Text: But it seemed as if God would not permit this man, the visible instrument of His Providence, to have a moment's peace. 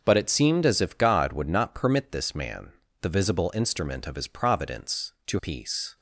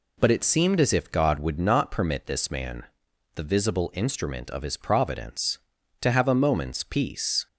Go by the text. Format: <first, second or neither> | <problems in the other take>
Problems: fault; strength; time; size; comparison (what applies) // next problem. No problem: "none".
second | skips "have a moment's"; at 5.3 s